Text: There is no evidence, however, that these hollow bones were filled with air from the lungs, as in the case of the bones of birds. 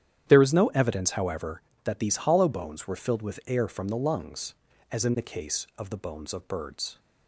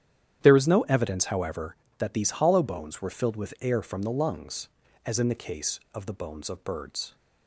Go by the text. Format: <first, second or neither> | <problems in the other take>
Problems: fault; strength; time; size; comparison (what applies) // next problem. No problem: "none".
neither | starts louder than the rest; strong; the same in both